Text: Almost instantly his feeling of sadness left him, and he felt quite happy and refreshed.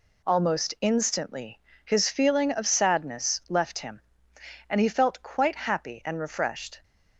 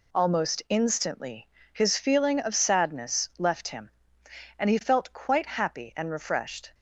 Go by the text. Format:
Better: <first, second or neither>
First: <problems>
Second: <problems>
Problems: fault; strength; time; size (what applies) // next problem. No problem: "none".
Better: neither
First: pauses between "instantly" and "his"; slight; at 1.5 s; 0.26 s long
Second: pauses between "instantly" and "his"; slight; at 1.4 s; 0.26 s long